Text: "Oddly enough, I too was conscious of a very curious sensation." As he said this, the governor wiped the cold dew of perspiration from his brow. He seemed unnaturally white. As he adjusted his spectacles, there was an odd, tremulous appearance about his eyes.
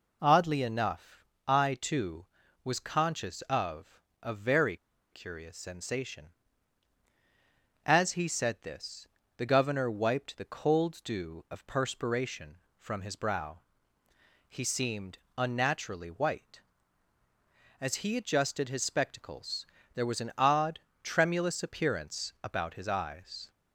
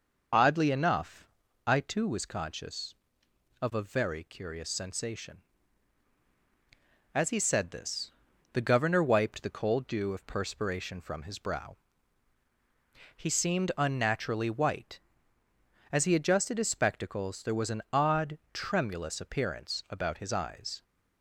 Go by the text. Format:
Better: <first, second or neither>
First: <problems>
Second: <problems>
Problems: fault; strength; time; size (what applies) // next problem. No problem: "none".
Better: second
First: pauses between "of" and "a"; slight; at 3.9 s; 0.20 s long // pauses between "very" and "curious"; slight; at 4.7 s; 0.35 s long // pauses between "seemed" and "unnaturally"; slight; at 15.1 s; 0.18 s long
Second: none